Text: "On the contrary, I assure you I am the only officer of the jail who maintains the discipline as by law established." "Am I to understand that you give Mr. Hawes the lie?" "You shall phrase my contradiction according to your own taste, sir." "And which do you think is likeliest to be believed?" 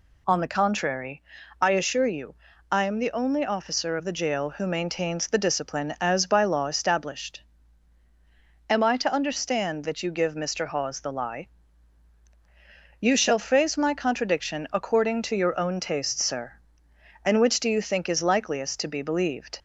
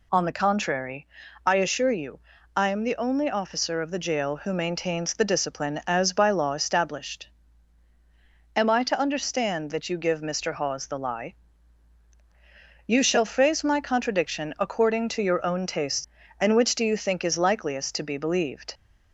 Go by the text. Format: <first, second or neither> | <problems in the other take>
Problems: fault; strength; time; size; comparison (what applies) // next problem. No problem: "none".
first | pauses between "you" and "I"; at 2.1 s; 0.38 s long; also in the first // skips "sir"; at 16.2 s